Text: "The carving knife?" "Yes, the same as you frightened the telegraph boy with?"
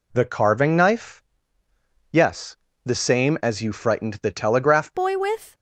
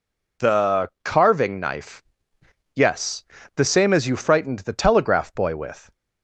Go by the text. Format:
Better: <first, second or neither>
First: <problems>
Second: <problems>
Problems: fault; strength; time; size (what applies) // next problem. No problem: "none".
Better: second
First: changes voice at "boy"; from 4.9 s on; 0.6 s long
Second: none